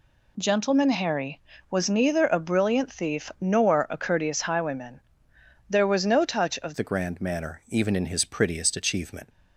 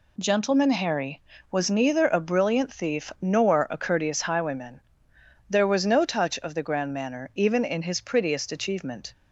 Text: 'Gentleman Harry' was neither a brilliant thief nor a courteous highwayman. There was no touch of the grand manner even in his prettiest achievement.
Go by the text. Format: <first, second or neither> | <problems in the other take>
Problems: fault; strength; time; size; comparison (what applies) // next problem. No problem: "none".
second | changes voice at "the"; from 6.7 s on; 2.5 s long